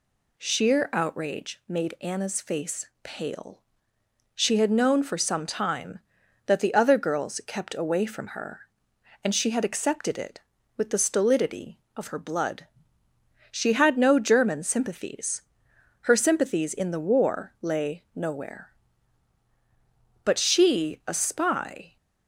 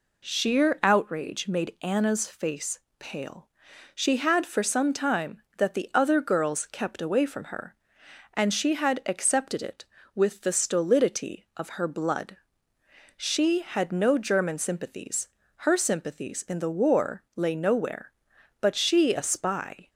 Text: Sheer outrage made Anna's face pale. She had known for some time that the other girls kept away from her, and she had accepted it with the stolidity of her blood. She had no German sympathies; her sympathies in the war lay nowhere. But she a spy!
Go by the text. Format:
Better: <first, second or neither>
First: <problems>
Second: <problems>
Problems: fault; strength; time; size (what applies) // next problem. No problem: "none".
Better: first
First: pauses between "face" and "pale"; slight; at 2.8 s; 0.16 s long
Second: pauses between "face" and "pale"; slight; at 2.7 s; 0.18 s long // skips "known"; at 4.4 s